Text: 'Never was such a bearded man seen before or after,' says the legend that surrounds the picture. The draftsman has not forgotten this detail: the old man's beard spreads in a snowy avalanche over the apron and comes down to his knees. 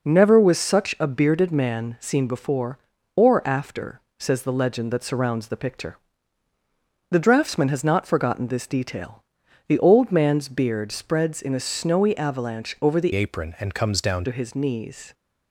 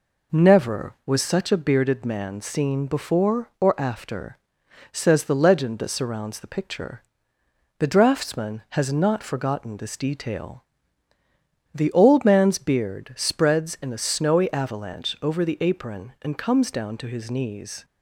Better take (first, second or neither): second